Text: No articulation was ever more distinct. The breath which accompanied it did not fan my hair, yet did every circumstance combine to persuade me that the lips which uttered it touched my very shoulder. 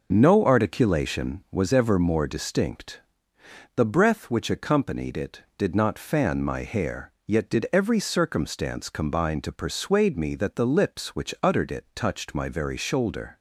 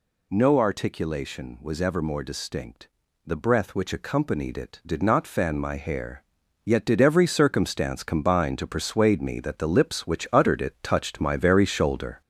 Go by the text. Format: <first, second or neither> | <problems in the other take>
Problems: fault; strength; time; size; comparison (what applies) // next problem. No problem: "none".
first | gets louder; noticeable; throughout; 5 dB